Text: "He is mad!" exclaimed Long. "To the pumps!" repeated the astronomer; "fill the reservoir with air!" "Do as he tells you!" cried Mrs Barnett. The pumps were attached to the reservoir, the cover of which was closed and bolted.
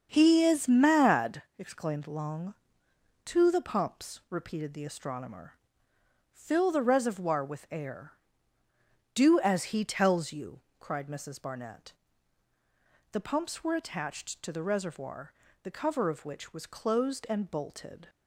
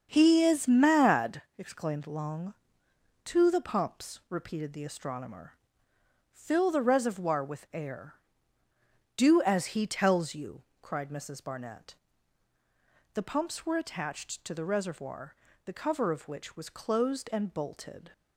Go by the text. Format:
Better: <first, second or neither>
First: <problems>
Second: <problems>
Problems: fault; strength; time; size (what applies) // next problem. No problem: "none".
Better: neither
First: starts louder than the rest; strong; until 1.1 s; 7.5 dB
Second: starts louder than the rest; strong; until 1.1 s; 7.5 dB